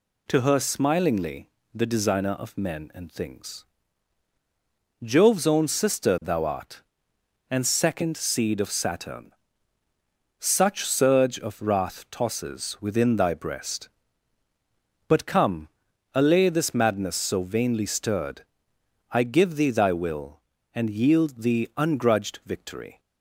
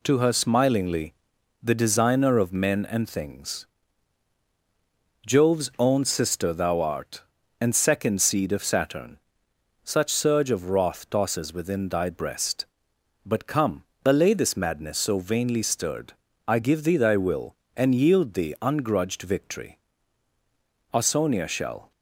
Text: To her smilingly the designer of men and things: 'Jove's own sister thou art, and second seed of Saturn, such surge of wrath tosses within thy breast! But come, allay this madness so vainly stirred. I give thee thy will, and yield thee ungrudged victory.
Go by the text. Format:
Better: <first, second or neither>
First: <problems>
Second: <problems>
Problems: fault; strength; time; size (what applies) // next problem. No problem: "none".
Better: first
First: pauses between "smilingly" and "the"; slight; at 1.5 s; 0.24 s long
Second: pauses between "smilingly" and "the"; noticeable; at 1.1 s; 0.48 s long // goes on to say "Ausonia shall"; noticeable; from 20.9 s on; 0.98 s long